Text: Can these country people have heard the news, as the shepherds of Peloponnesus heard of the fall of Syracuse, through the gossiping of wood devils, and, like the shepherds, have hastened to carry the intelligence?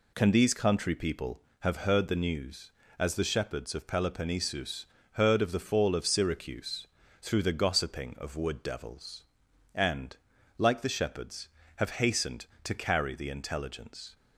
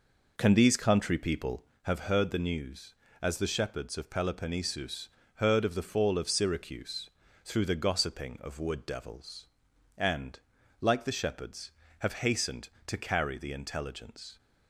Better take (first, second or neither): first